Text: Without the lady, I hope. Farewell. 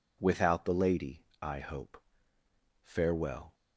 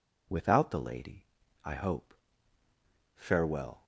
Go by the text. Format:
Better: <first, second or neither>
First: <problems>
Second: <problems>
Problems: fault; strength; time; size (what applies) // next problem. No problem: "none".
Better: neither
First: none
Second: none